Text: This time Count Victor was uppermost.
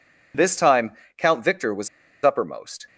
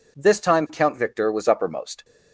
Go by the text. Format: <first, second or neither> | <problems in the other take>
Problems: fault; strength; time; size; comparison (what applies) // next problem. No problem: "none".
second | pauses between "time" and "Count"; slight; at 0.9 s; 0.24 s long // pauses between "was" and "uppermost"; slight; at 1.8 s; 0.35 s long